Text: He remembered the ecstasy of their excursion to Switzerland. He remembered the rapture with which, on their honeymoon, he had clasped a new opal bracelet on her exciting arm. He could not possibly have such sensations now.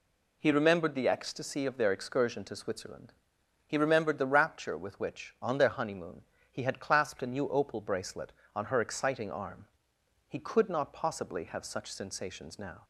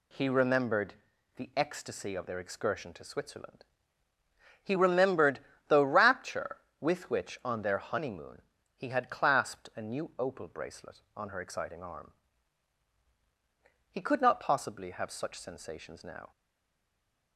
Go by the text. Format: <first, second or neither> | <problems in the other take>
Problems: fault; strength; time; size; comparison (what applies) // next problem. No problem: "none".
first | pauses between "remembered" and "the"; at 0.9 s; 0.44 s long // pauses between "remembered" and "the"; slight; at 5.3 s; 0.30 s long // stays silent after the last word; from 16.3 s on; 1.0 s long